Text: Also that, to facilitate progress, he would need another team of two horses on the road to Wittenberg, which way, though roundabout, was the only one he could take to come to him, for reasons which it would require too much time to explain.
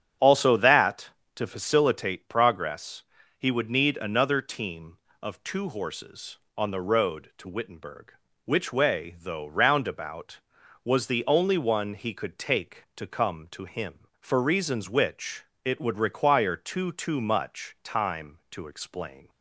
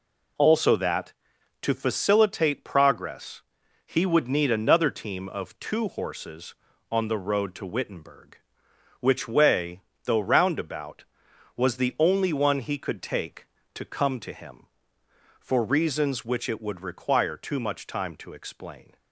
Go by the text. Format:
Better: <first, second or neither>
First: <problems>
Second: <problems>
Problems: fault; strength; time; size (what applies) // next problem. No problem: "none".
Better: second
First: starts louder than the rest; strong; until 1.4 s; 8 dB // pauses between "which" and "it"; slight; at 15.4 s; 0.18 s long // says "too" twice; at 16.9 s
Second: none